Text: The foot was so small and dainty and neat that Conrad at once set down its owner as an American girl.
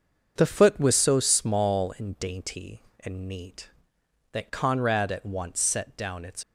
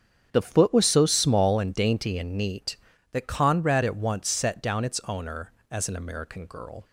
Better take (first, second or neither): second